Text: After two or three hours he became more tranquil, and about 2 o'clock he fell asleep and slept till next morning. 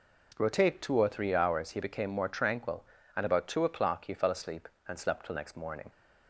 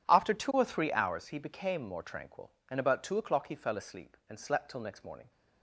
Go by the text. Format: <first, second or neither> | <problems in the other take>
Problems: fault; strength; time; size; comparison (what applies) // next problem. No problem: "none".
second | says "Rotate" for "After"; at 0.3 s